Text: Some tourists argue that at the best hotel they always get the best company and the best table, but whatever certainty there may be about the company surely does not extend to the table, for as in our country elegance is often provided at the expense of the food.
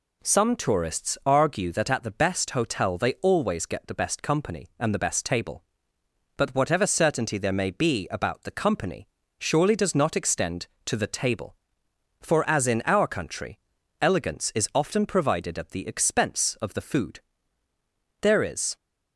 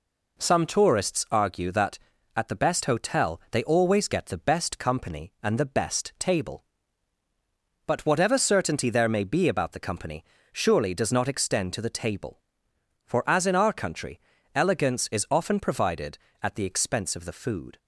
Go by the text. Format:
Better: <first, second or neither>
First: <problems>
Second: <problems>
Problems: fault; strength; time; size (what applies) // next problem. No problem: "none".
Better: second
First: pauses between "company" and "surely"; slight; at 9.0 s; 0.30 s long // pauses between "country" and "elegance"; at 13.5 s; 0.42 s long // goes on to say "There is"; from 18.2 s on; 0.54 s long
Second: pauses between "company" and "surely"; slight; at 10.2 s; 0.28 s long // pauses between "country" and "elegance"; slight; at 14.1 s; 0.34 s long